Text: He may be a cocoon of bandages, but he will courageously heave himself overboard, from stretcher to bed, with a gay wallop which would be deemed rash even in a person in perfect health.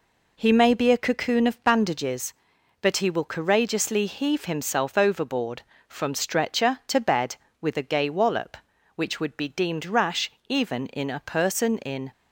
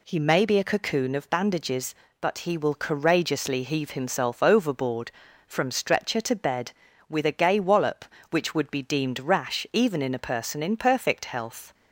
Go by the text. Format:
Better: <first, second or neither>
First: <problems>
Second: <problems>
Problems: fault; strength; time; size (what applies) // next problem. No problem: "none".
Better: second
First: pauses between "rash" and "even"; slight; at 10.2 s; 0.18 s long // stops before "perfect health"; at 12.1 s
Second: none